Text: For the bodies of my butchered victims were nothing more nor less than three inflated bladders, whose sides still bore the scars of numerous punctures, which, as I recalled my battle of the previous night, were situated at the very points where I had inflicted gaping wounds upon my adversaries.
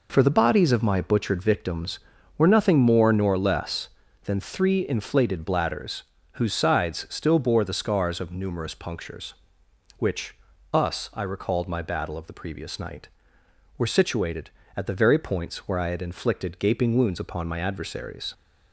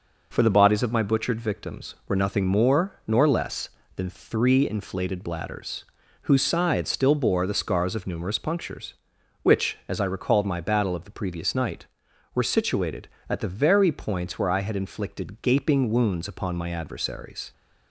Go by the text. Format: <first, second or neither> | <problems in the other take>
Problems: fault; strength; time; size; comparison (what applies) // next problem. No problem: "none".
second | says "us" for "as"; at 10.7 s